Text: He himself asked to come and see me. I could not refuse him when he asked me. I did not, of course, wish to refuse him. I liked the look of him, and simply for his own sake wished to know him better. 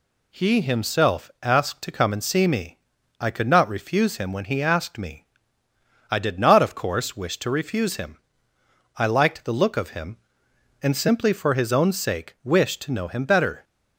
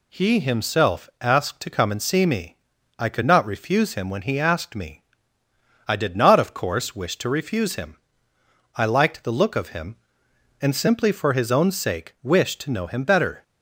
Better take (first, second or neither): neither